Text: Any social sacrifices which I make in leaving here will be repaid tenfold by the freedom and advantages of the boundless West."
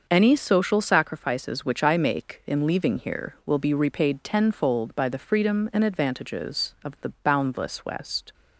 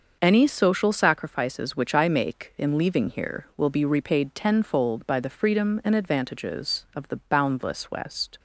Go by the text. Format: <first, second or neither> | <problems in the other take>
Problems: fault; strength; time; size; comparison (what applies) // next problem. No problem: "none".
neither | starts louder than the rest; the same in both